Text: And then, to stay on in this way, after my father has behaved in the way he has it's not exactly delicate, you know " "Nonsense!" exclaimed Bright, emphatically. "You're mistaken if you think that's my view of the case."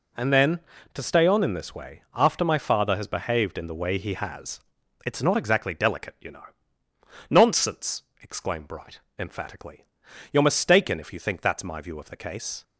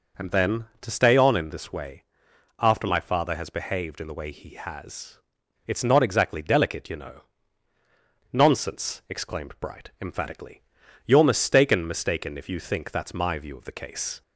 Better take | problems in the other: first | pauses between "has" and "it's"; noticeable; at 5.1 s; 0.48 s long; noticeable in the first // says "mistaken" twice; at 11.8 s

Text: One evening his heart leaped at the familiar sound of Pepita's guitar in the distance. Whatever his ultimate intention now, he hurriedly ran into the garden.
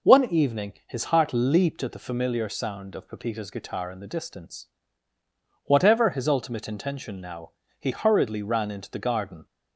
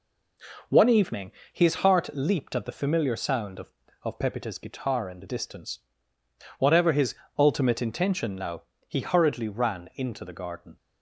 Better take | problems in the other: first | pauses between "evening" and "his"; slight; at 1.3 s; 0.20 s long // says "of" twice; at 4.0 s // pauses between "his" and "ultimate"; slight; at 7.1 s; 0.24 s long

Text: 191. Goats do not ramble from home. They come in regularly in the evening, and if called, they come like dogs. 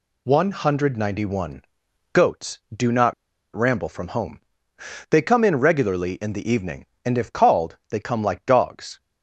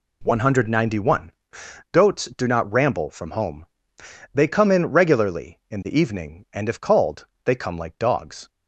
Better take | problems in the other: second | pauses between "not" and "ramble"; at 3.1 s; 0.41 s long

